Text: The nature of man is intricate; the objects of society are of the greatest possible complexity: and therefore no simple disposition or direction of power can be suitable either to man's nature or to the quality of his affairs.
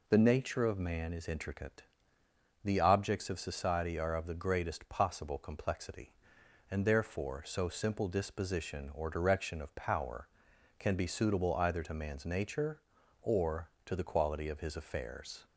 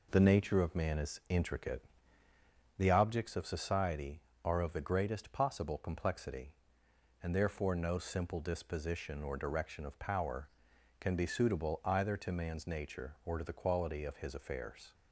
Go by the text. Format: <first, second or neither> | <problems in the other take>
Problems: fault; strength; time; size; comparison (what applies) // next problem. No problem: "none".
second | says "so" for "no"; at 7.4 s